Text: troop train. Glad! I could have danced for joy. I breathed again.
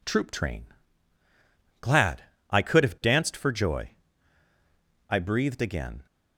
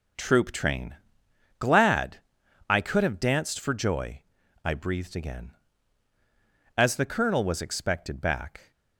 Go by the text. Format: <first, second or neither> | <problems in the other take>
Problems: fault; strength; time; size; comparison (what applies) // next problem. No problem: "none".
first | goes on to say "As the Colonel was expected back"; strong; from 6.7 s on; 1.9 s long